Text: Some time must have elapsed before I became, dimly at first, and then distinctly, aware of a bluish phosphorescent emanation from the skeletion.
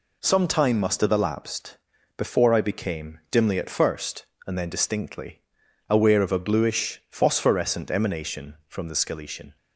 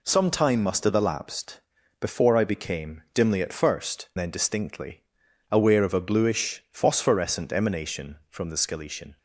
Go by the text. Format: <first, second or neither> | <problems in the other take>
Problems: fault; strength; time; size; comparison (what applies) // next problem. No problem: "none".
first | pauses between "elapsed" and "before"; at 1.6 s; 0.40 s long; also in the first // skips "and"; at 4.1 s